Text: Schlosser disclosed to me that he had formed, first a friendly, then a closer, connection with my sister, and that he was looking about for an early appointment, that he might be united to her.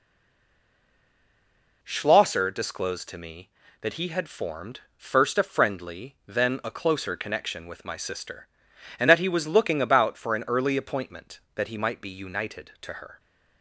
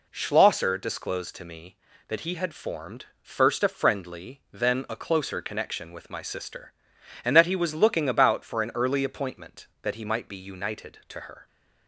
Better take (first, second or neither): second